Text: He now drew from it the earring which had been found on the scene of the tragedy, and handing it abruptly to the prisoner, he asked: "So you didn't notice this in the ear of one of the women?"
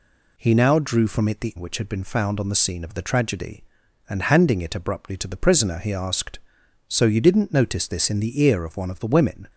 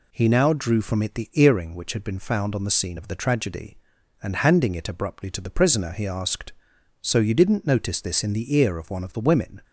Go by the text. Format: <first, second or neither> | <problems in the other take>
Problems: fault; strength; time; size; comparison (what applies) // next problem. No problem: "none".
second | skips "earring"; at 1.5 s